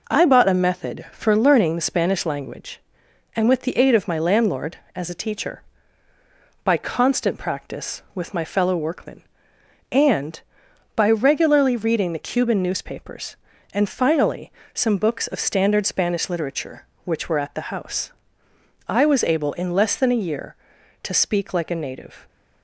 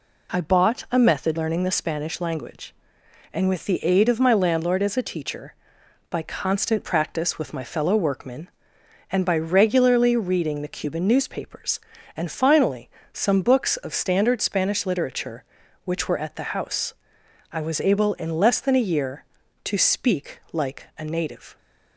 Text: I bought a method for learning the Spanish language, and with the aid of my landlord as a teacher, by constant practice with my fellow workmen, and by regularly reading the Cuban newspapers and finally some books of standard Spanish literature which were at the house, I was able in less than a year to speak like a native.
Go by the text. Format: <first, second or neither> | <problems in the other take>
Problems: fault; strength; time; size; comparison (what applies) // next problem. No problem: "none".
first | skips "for"; at 1.3 s // pauses between "finally" and "some"; slight; at 12.8 s; 0.22 s long; slight in the first